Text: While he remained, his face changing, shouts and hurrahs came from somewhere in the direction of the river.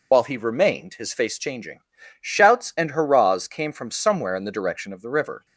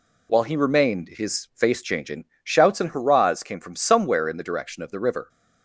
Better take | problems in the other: second | loses the start of "While"; at 0.1 s; 85 ms

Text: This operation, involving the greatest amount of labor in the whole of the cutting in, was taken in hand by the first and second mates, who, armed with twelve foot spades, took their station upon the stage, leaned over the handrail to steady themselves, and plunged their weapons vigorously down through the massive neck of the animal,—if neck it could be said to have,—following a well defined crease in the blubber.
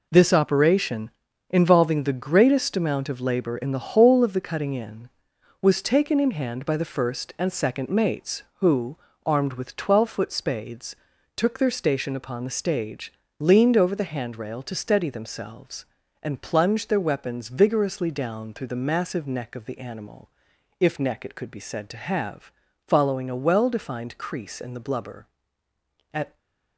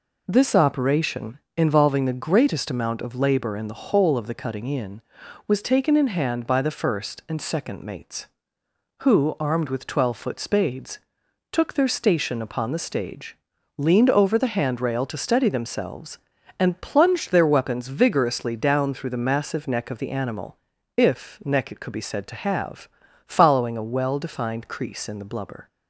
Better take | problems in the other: second | goes on to say "At"; slight; from 26.1 s on; 0.24 s long // stays silent after the last word; slight; from 26.2 s on; 0.5 s long

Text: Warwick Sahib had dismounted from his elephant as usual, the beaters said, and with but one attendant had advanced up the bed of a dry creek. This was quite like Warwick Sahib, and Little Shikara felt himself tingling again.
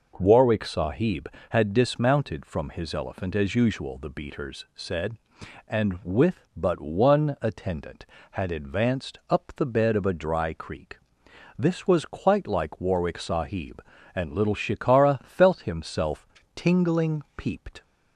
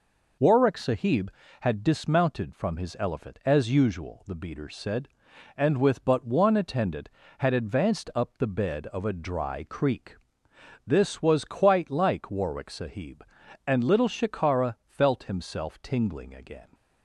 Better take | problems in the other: second | pauses between "himself" and "tingling"; slight; at 16.2 s; 0.28 s long // says "peeped" for "again"; at 17.3 s

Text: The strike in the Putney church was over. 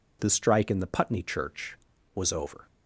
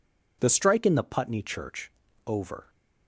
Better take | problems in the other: first | skips "was"; at 2.0 s

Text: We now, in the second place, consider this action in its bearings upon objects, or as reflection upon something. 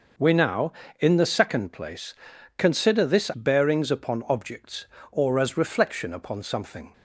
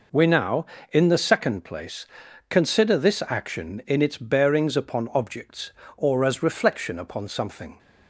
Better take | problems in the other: second | skips "action in its"; at 3.3 s

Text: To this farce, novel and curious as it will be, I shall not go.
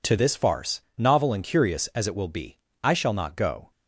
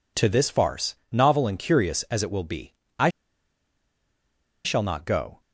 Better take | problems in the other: first | pauses between "I" and "shall"; strong; at 3.0 s; 1.5 s long

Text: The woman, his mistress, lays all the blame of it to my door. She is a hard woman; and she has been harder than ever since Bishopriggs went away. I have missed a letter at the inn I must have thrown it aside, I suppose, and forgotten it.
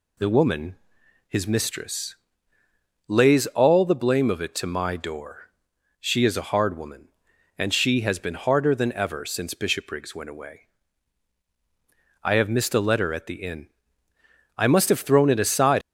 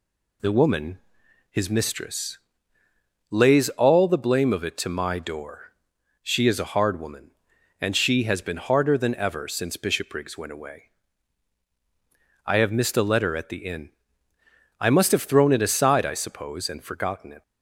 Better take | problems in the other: second | pauses between "inn" and "I"; noticeable; at 13.6 s; 0.90 s long; noticeable in the second // stops before "I suppose and forgotten it"; at 15.8 s

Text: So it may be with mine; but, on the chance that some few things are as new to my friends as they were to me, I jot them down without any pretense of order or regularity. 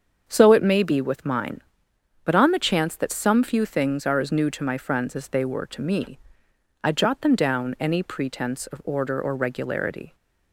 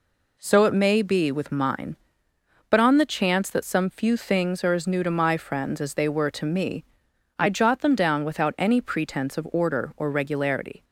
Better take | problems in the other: second | starts louder than the rest; until 1.2 s; 7 dB // skips "without"; at 7.7 s

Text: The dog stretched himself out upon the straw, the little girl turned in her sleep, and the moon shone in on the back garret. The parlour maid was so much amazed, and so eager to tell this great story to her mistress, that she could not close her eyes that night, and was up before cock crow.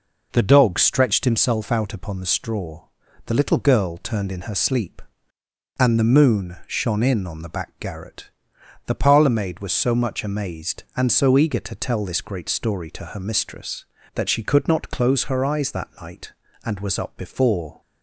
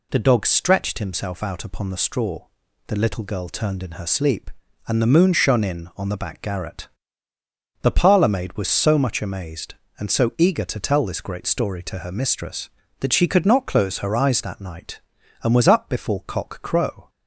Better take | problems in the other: second | stops before "cock crow"; at 17.8 s

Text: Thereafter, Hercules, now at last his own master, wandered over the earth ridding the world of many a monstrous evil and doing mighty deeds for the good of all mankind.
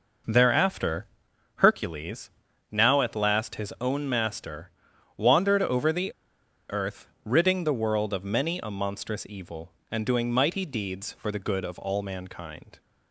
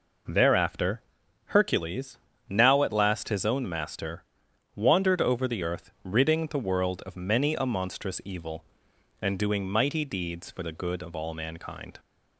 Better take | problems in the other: second | pauses between "the" and "earth"; noticeable; at 6.1 s; 0.57 s long // pauses between "earth" and "ridding"; slight; at 7.0 s; 0.16 s long

